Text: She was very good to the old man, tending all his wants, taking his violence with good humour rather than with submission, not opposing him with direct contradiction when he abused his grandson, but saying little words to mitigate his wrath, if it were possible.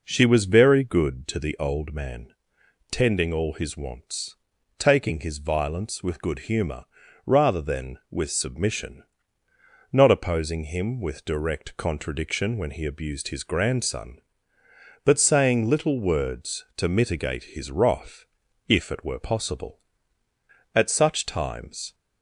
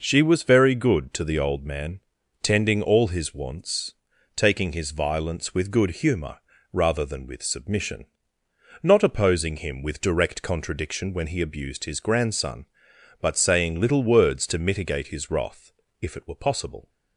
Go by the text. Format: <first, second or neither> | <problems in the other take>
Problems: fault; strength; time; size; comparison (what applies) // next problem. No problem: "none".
second | pauses between "humour" and "rather"; at 6.8 s; 0.40 s long; slight in the second // goes on to say "At such times"; noticeable; from 20.7 s on; 1.2 s long